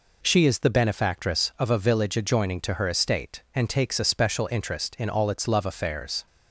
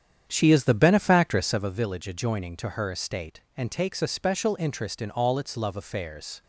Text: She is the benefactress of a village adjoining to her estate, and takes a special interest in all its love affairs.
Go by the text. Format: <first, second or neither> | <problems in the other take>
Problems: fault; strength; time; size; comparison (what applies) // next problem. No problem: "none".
first | starts louder than the rest; strong; until 1.8 s; 8.5 dB